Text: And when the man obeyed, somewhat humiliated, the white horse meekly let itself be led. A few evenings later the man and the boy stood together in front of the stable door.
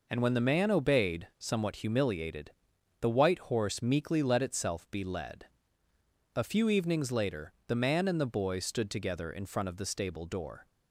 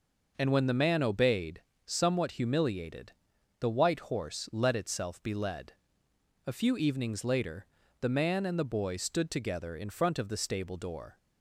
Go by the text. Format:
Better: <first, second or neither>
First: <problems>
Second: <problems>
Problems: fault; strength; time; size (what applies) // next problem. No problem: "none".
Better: first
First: none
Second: skips "meekly"; at 4.4 s // pauses between "later" and "the"; slight; at 7.6 s; 0.36 s long